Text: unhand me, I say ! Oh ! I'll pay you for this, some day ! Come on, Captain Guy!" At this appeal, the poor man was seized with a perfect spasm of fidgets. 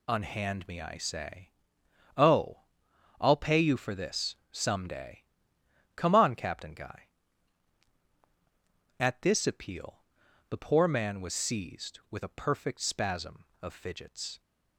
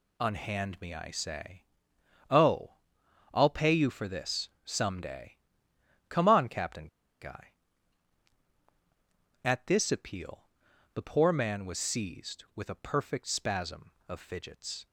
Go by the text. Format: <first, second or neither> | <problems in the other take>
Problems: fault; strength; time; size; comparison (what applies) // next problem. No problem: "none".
first | pauses between "Captain" and "Guy"; slight; at 6.8 s; 0.34 s long